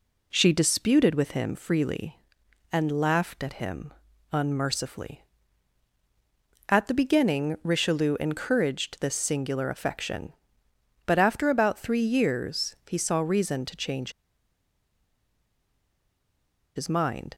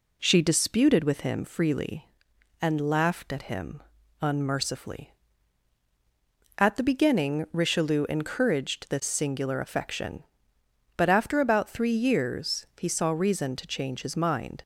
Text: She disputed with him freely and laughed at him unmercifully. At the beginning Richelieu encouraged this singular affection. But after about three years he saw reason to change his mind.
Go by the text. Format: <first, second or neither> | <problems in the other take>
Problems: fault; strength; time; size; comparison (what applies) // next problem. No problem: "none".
second | pauses between "him" and "unmercifully"; at 3.9 s; 0.40 s long; also in the second // pauses between "change" and "his"; strong; at 14.1 s; 2.6 s long